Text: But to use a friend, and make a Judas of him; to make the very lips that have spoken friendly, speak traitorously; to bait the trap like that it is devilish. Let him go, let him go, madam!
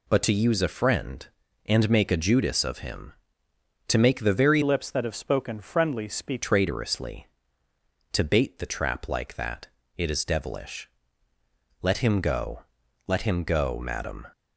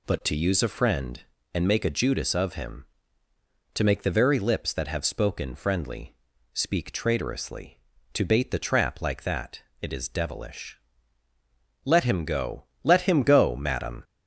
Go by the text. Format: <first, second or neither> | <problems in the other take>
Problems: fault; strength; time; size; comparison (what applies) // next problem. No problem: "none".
second | changes voice from "lips" to "speak"; from 4.6 to 6.4 s; 1.8 s long // pauses between "that" and "it"; slight; at 9.6 s; 0.28 s long; slight in the second